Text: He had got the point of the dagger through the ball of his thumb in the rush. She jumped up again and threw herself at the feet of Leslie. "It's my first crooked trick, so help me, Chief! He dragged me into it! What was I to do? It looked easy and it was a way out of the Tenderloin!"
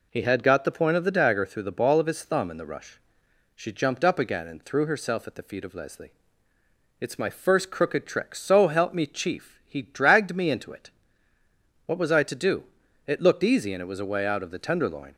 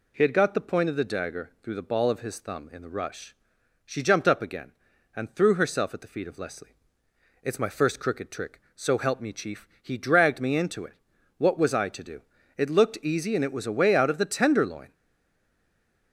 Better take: first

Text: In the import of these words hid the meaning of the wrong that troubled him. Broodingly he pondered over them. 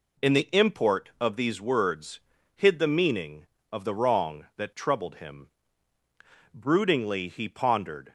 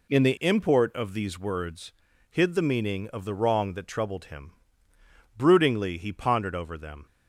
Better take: second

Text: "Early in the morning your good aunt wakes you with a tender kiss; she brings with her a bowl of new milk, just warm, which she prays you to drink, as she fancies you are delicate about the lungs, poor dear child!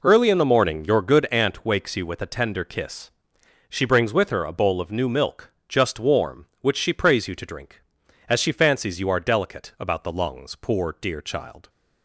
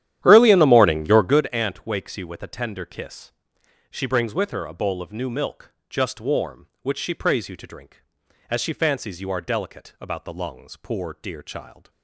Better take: first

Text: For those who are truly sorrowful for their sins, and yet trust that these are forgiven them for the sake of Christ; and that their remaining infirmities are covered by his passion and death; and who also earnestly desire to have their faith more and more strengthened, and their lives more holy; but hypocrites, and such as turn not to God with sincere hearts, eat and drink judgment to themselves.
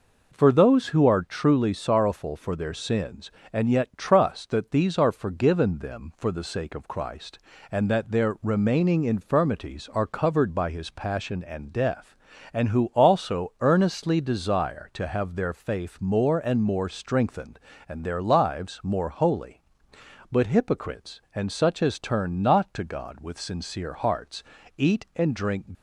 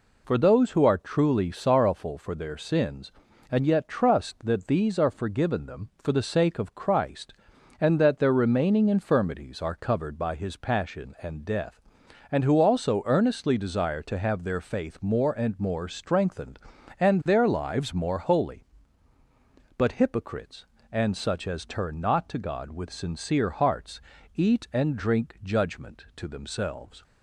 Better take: second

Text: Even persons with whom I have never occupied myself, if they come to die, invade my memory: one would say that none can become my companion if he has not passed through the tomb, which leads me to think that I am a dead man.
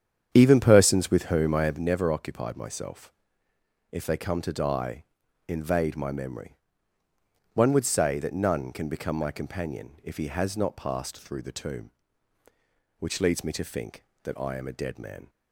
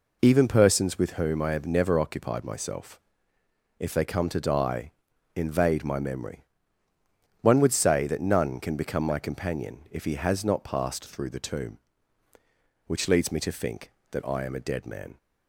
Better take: second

